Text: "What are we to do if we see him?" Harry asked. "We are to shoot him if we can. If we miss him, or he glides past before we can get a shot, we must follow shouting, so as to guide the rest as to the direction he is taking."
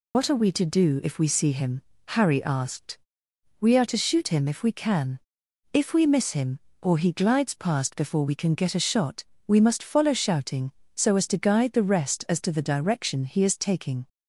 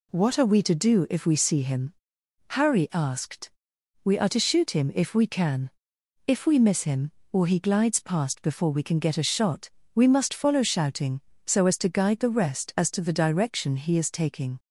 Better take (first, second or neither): second